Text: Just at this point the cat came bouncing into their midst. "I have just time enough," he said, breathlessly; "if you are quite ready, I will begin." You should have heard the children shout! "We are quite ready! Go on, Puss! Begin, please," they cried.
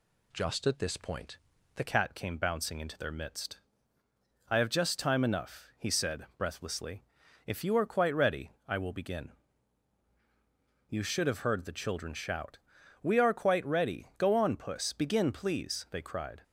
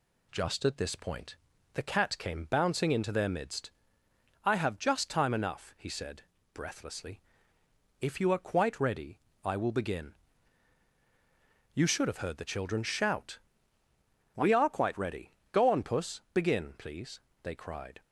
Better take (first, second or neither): second